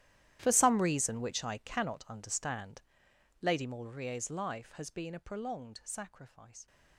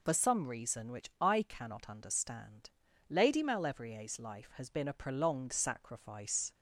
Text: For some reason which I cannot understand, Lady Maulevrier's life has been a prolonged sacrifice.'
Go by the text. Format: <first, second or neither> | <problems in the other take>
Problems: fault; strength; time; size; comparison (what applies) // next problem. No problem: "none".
second | gets quieter; strong; throughout; 18.5 dB